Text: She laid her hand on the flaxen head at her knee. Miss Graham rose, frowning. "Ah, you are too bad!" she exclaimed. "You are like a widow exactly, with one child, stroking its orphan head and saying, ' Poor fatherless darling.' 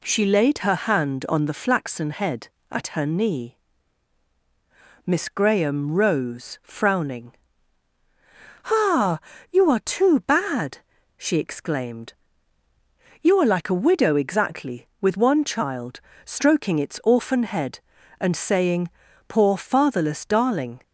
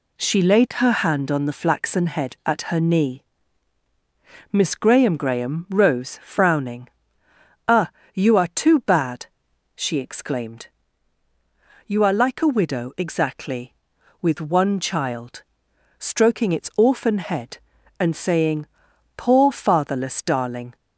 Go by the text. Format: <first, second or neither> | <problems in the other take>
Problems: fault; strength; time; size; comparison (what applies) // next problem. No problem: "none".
first | says "Graham" twice; at 5.1 s